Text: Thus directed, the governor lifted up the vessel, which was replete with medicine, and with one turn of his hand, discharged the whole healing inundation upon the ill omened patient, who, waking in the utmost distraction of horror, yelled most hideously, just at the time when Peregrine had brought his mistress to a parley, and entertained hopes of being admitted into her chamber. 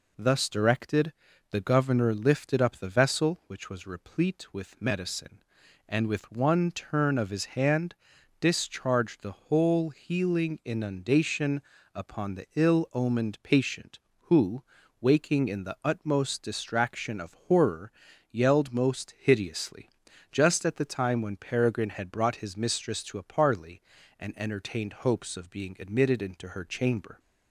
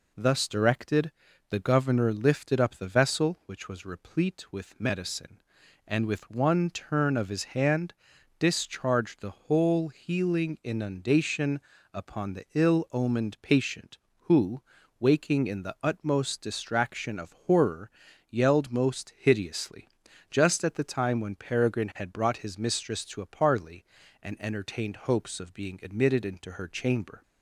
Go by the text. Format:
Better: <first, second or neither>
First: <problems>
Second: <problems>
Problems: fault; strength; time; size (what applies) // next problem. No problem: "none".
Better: neither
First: pauses between "inundation" and "upon"; slight; at 11.6 s; 0.34 s long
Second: pauses between "inundation" and "upon"; slight; at 11.5 s; 0.34 s long